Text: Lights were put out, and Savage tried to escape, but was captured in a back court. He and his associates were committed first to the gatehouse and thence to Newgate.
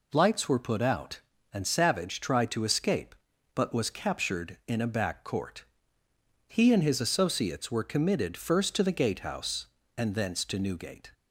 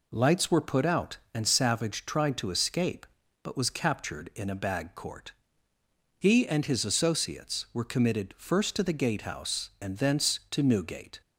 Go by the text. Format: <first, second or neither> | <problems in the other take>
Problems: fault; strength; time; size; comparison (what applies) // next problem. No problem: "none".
first | says "bag" for "back"; at 4.5 s